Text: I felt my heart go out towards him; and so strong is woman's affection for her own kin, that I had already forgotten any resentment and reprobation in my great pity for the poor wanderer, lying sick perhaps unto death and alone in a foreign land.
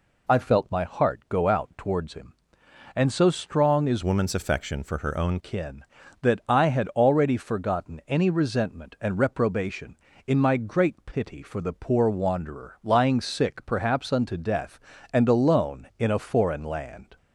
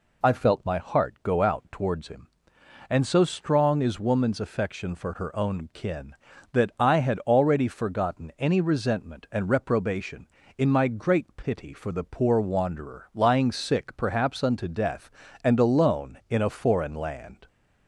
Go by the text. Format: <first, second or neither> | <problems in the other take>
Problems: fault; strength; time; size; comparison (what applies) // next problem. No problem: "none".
second | changes voice from "woman's" to "own"; from 4.0 to 5.3 s; 1.3 s long